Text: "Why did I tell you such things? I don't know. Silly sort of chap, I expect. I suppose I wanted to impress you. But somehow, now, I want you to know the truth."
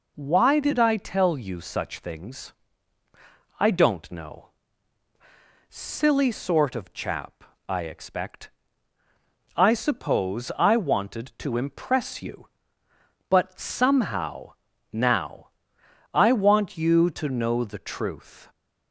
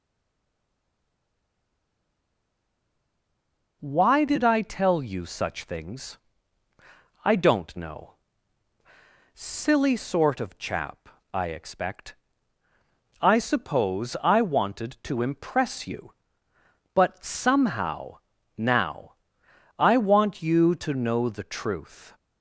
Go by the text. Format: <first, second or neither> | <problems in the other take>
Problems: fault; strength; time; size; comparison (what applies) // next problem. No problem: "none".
first | stays silent before the first word; strong; until 3.8 s; 3.8 s long